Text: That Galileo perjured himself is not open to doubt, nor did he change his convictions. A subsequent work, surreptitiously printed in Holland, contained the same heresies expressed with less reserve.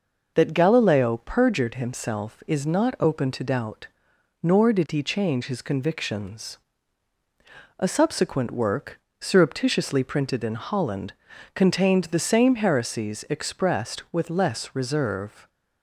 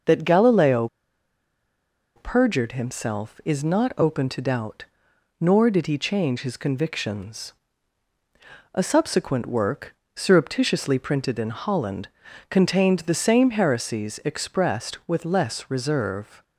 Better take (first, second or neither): first